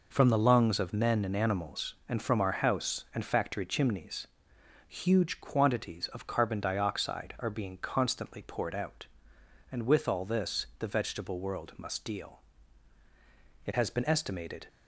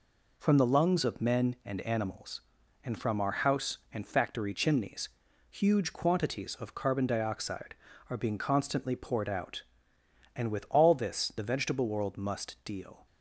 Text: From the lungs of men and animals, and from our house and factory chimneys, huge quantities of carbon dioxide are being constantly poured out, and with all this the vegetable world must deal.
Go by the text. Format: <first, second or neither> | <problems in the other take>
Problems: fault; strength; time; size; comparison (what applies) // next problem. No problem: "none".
second | goes on to say "It has been estimated"; noticeable; from 13.6 s on; 1.0 s long